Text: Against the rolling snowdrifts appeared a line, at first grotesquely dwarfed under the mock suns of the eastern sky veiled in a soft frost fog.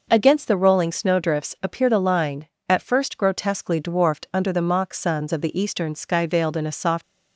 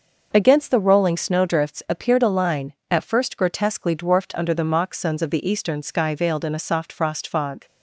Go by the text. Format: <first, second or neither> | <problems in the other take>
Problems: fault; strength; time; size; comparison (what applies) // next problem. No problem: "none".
second | stops before "frost fog"; at 7.0 s